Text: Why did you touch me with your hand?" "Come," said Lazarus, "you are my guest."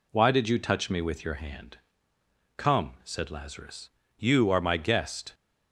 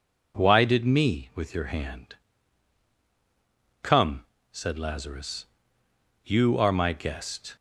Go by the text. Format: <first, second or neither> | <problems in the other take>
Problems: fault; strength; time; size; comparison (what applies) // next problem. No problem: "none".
first | skips "you touch"; at 0.8 s